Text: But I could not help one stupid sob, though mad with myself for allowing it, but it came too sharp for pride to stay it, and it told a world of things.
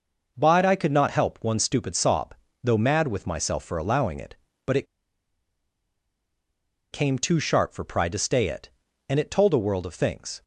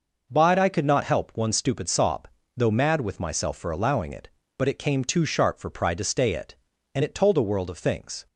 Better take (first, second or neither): second